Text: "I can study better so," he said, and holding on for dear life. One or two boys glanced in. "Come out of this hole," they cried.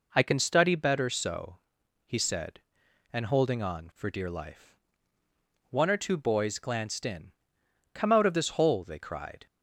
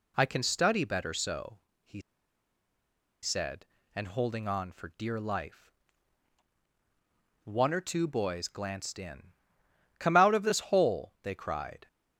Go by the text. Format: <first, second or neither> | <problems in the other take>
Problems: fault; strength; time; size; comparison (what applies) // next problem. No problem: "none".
first | pauses between "he" and "said"; at 2.0 s; 1.2 s long